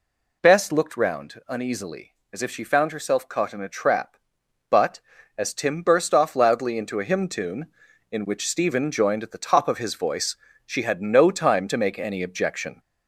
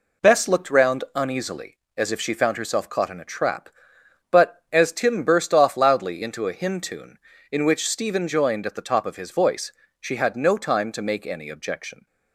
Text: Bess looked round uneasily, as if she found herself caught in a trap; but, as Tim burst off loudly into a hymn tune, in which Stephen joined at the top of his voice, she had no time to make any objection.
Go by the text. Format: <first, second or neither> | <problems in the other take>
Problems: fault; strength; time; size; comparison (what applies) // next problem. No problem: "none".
second | gets louder; slight; throughout; 3 dB